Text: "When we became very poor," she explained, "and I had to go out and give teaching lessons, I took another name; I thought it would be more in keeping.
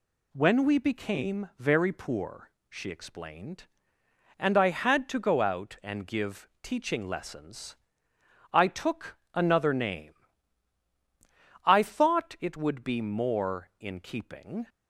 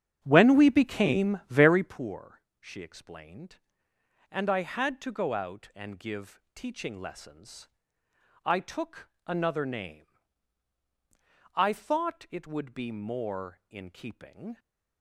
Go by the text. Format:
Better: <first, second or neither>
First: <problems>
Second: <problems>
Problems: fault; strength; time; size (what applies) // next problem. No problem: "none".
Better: first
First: pauses between "took" and "another"; slight; at 9.1 s; 0.18 s long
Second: starts louder than the rest; strong; until 2.0 s; 9 dB // pauses between "took" and "another"; slight; at 9.0 s; 0.18 s long